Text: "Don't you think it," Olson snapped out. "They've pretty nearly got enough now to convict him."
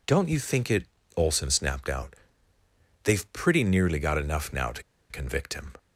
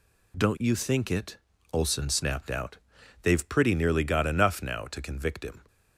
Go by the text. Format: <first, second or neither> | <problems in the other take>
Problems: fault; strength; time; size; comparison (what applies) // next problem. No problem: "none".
second | pauses between "to" and "convict"; slight; at 4.8 s; 0.27 s long